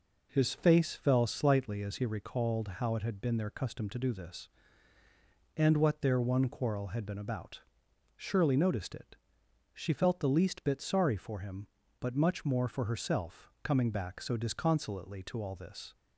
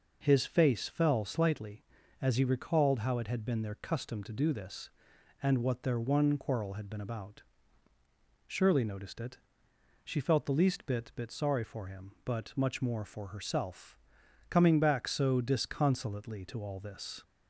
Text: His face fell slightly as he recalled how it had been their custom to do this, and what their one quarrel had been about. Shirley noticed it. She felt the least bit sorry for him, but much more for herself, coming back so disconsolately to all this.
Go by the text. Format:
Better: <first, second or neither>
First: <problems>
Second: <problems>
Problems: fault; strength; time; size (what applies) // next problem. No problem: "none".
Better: first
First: none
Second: says "bit" twice; at 11.1 s